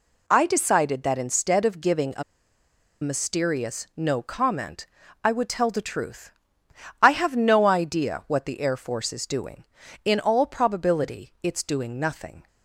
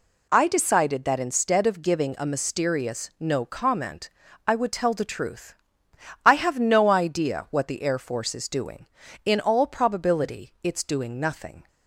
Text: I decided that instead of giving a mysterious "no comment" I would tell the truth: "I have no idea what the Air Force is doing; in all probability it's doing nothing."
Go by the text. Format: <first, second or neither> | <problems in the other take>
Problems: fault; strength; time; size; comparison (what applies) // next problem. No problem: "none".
second | pauses between "a" and "mysterious"; noticeable; at 2.2 s; 0.79 s long // pauses between "comment" and "I"; slight; at 4.8 s; 0.36 s long; slight in the second